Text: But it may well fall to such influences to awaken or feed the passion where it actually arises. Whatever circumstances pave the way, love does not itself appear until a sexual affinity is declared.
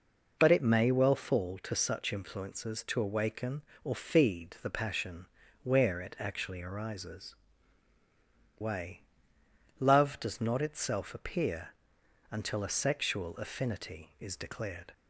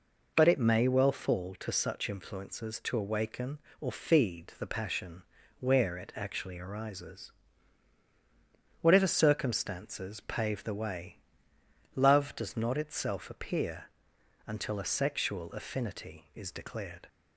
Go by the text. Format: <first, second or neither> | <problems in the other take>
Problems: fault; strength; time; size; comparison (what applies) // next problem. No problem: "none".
second | pauses between "passion" and "where"; at 5.2 s; 0.38 s long; also in the second // skips "Whatever circumstances pave the"; at 7.9 s // pauses between "appear" and "until"; noticeable; at 11.6 s; 0.62 s long; noticeable in the second